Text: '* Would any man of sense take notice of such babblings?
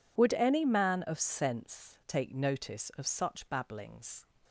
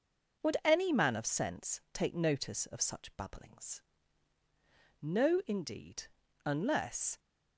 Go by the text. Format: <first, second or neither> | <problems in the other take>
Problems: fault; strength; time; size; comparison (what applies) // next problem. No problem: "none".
first | goes on to say "No indeed unless"; strong; from 5.0 s on; 2.1 s long